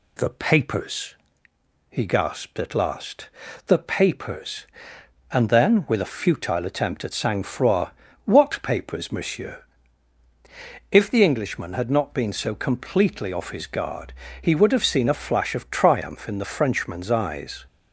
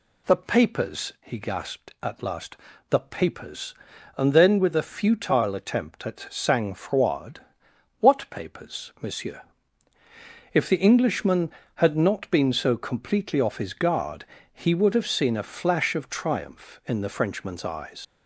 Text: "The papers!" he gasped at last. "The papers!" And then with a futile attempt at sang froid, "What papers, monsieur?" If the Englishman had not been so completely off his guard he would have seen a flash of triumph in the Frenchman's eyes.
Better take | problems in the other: first | pauses between "guard" and "he"; slight; at 14.2 s; 0.26 s long; slight in the first // leaves "eyes" unfinished; at 18.0 s; 90 ms

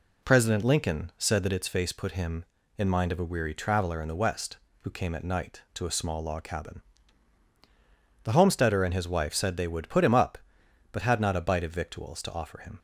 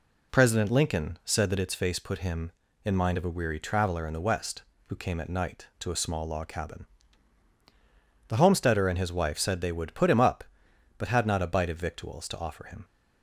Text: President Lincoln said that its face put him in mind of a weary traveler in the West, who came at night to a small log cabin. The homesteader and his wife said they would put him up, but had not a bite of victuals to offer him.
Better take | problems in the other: neither | none

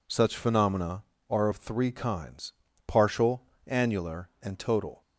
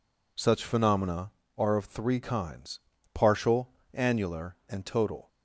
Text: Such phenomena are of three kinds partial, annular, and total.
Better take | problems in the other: neither | pauses between "kinds" and "partial"; slight; the same in both

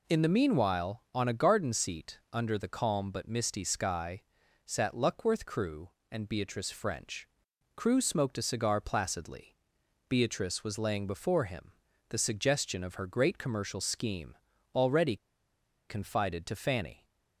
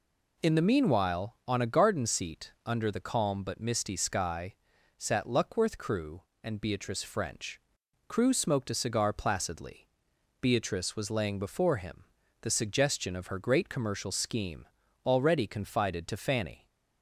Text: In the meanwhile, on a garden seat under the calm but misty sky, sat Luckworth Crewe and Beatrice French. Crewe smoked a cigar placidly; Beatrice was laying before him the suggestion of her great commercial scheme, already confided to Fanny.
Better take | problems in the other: second | pauses between "him" and "the"; at 11.7 s; 0.40 s long; also in the second // pauses between "already" and "confided"; noticeable; at 15.1 s; 0.71 s long

